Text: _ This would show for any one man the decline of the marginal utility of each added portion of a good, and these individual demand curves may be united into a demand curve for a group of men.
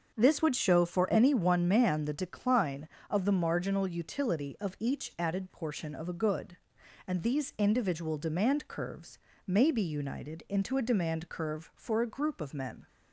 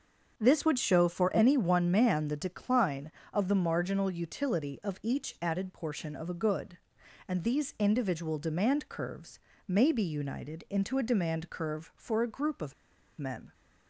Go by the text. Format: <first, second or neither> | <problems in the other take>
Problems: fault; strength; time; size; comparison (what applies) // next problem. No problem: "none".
first | starts louder than the rest; until 1.3 s; 6.5 dB; also in the first // pauses between "curves" and "may"; slight; at 9.3 s; 0.26 s long; slight in the first // pauses between "of" and "men"; at 12.7 s; 0.44 s long